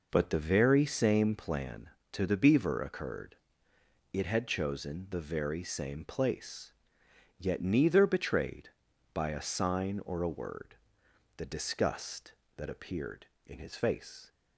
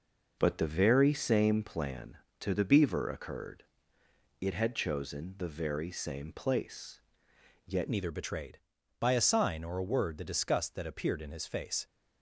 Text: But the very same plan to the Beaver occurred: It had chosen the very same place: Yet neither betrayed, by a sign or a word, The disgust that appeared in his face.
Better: first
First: none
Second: changes voice at "neither"; from 7.8 s on; 4.0 s long

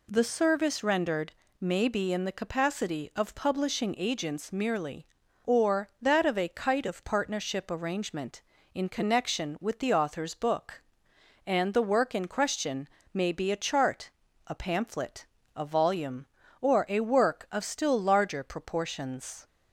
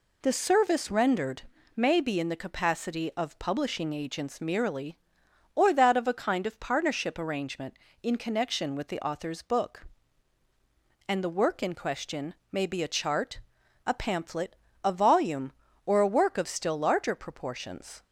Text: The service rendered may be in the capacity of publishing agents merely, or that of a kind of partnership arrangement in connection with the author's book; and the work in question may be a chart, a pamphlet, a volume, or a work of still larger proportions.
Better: second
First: pauses between "rendered" and "may"; slight; at 1.3 s; 0.28 s long // says "kite" for "kind"; at 6.4 s // pauses between "question" and "may"; slight; at 12.8 s; 0.24 s long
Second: pauses between "rendered" and "may"; slight; at 1.4 s; 0.34 s long // pauses between "question" and "may"; slight; at 12.3 s; 0.16 s long

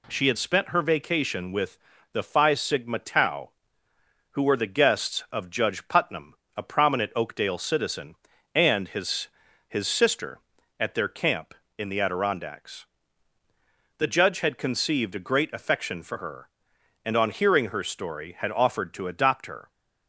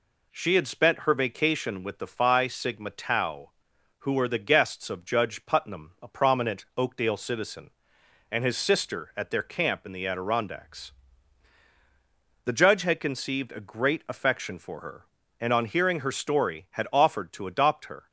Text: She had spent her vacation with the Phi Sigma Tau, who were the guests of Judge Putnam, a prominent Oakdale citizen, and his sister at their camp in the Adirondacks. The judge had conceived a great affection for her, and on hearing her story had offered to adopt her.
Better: second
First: pauses between "with" and "the"; slight; at 1.7 s; 0.34 s long // says "his" twice; at 9.6 s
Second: none

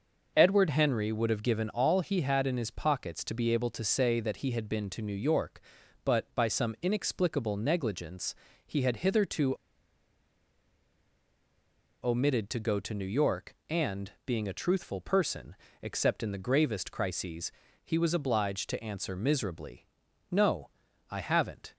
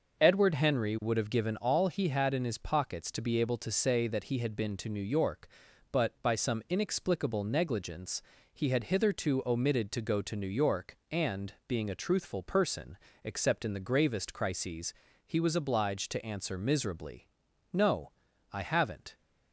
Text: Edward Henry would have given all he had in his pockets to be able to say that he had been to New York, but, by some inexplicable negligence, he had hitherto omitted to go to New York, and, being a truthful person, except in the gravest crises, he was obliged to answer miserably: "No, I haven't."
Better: second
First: pauses between "hitherto" and "omitted"; strong; at 9.5 s; 2.4 s long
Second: none

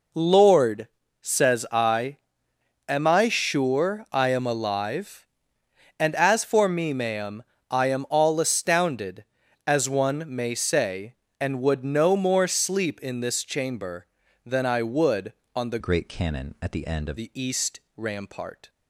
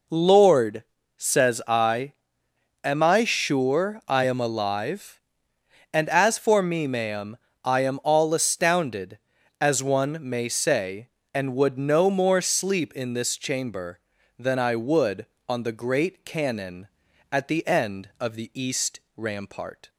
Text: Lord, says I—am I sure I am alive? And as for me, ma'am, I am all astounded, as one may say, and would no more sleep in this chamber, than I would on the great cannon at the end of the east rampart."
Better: second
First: changes voice from "great" to "of"; from 15.7 to 17.1 s; 1.4 s long // pauses between "east" and "rampart"; slight; at 17.7 s; 0.16 s long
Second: pauses between "east" and "rampart"; slight; at 18.9 s; 0.16 s long

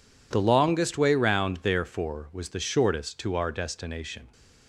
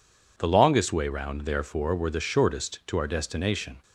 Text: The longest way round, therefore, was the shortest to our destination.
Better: first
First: none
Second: says "were" for "was"; at 1.9 s

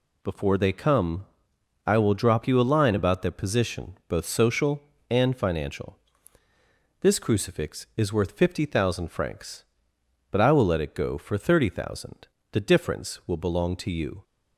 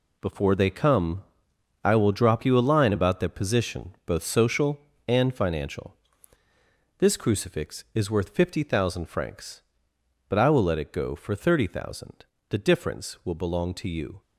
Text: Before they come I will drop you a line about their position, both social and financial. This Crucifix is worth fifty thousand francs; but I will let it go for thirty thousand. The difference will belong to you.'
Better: first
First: pauses between "come" and "I"; noticeable; at 1.2 s; 0.62 s long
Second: gets quieter; strong; throughout; 10 dB // pauses between "come" and "I"; noticeable; at 1.2 s; 0.62 s long

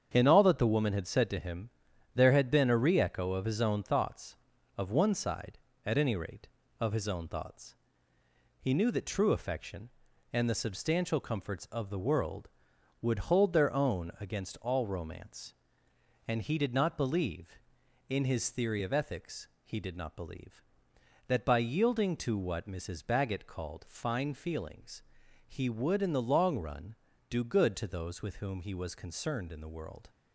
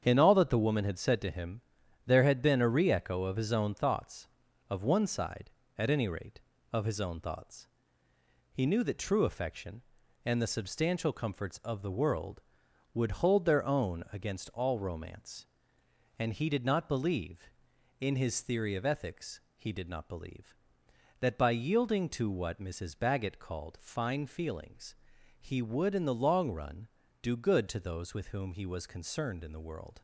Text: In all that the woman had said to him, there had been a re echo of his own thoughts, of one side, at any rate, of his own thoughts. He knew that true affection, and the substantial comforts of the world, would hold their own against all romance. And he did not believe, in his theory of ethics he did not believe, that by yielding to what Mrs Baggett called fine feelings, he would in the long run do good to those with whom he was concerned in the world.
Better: neither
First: starts louder than the rest; strong; until 1.1 s; 8 dB // pauses between "ethics" and "he"; slight; at 19.4 s; 0.16 s long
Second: starts louder than the rest; strong; until 1.0 s; 8 dB // pauses between "ethics" and "he"; slight; at 19.4 s; 0.16 s long

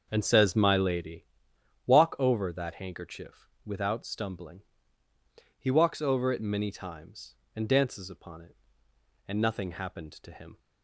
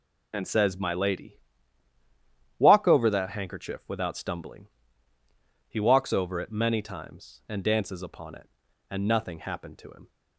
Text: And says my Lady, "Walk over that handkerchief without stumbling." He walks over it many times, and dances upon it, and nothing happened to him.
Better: second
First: starts louder than the rest; until 1.1 s; 6.5 dB // pauses between "handkerchief" and "without"; slight; at 3.4 s; 0.16 s long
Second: none

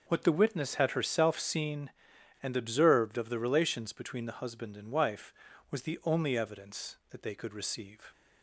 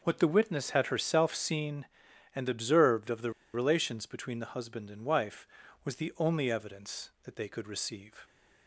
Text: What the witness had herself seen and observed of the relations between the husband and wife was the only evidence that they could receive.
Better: first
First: none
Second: pauses between "the" and "relations"; slight; at 3.3 s; 0.23 s long

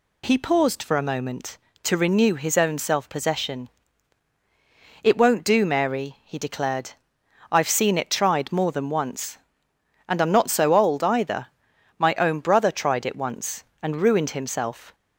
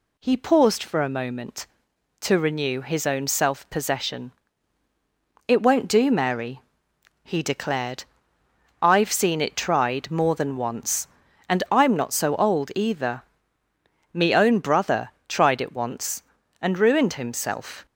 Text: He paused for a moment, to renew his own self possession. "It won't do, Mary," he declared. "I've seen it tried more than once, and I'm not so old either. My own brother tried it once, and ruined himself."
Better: first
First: none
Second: says "Me" for "My"; at 14.1 s // pauses between "brother" and "tried"; slight; at 15.1 s; 0.16 s long

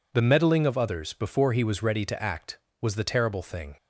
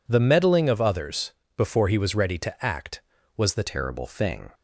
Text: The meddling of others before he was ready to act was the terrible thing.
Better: first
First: none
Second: pauses between "others" and "before"; slight; at 1.3 s; 0.24 s long // changes voice at "terrible"; from 3.6 s on; 0.9 s long

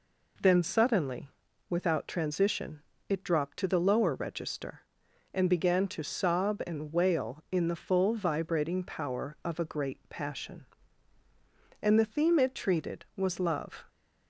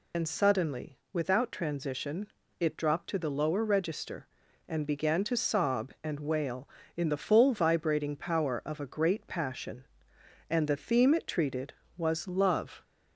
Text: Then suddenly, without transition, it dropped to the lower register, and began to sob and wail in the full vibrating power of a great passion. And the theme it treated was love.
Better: first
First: none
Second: loses the start of "Then"; at 0.1 s; 80 ms

